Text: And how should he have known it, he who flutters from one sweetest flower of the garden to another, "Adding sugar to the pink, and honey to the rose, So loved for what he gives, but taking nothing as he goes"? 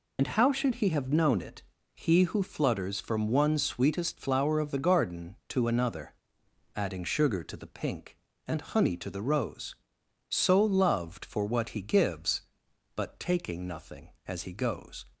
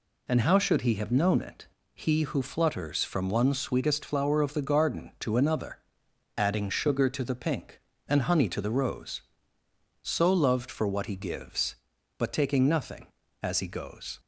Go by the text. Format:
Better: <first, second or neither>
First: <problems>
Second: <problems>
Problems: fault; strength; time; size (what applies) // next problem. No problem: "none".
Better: second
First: loses the start of "And"; at 0.1 s; 65 ms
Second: none